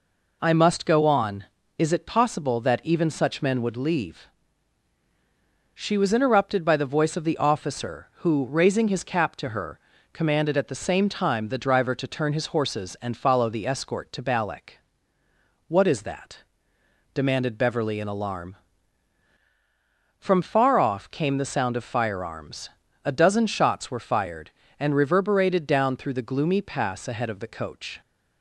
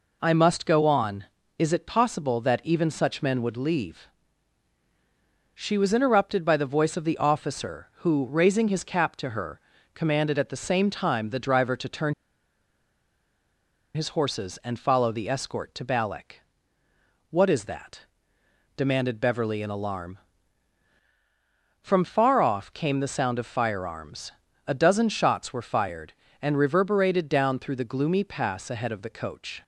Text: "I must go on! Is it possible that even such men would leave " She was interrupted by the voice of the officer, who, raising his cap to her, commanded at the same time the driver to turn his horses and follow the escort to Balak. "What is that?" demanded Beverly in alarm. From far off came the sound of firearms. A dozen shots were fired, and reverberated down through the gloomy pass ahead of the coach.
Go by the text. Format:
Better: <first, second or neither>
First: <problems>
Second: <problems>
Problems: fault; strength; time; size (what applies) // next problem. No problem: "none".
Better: first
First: none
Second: pauses between "turn" and "his"; strong; at 12.1 s; 1.8 s long